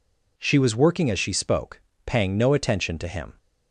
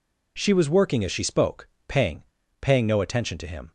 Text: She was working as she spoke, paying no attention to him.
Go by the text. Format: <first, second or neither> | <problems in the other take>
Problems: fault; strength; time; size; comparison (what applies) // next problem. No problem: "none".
first | says "paying" twice; at 2.6 s